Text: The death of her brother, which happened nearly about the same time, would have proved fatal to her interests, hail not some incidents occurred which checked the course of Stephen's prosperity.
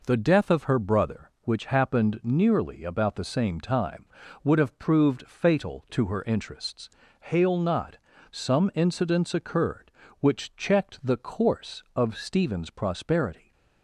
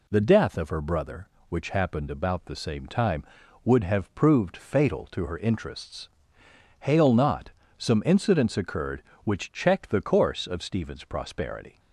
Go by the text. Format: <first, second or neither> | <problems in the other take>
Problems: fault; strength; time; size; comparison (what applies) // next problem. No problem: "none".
first | skips "nearly"; at 2.1 s // pauses between "not" and "some"; slight; at 7.4 s; 0.30 s long; slight in the first